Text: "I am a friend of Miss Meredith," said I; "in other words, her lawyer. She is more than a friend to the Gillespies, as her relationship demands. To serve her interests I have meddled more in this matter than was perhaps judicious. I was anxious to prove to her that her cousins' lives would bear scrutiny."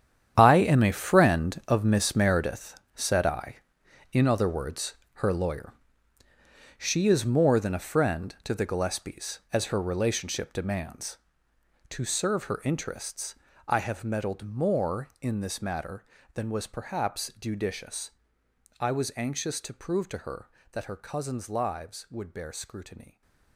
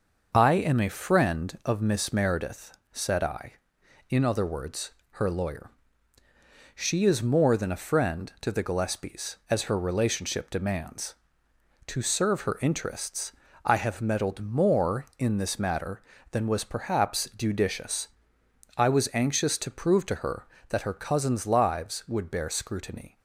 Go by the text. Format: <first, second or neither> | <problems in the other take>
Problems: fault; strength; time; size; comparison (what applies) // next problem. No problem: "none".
second | gets quieter; strong; throughout; 14 dB // starts louder than the rest; strong; until 1.3 s; 9.5 dB; noticeable in the second // pauses between "interests" and "I"; slight; at 13.3 s; 0.34 s long; slight in the second